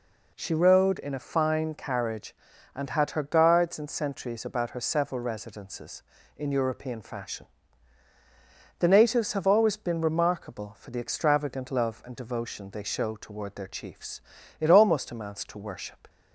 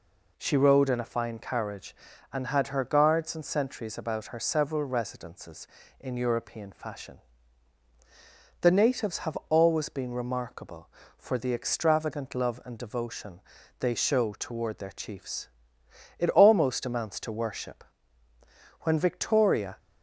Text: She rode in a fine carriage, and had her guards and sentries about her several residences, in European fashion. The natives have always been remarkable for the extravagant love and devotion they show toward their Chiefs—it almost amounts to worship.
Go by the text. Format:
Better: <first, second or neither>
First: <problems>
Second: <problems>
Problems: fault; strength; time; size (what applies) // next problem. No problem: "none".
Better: first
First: none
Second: pauses between "devotion" and "they"; at 13.4 s; 0.38 s long // goes on to say "When Victoria"; noticeable; from 18.7 s on; 0.98 s long